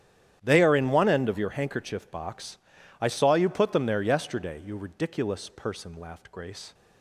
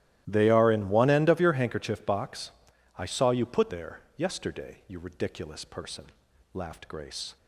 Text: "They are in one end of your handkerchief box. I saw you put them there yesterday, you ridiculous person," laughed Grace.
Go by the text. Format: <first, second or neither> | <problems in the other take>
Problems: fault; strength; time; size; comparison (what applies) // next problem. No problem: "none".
first | starts louder than the rest; strong; until 1.2 s; 14 dB; strong in the first // skips "them"; at 3.6 s // pauses between "there" and "yesterday"; slight; at 4.0 s; 0.16 s long